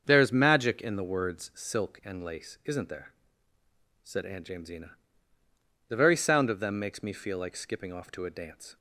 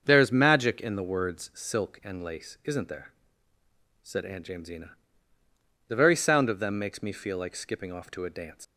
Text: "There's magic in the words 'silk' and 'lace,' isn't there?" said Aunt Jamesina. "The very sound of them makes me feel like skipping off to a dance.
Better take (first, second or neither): first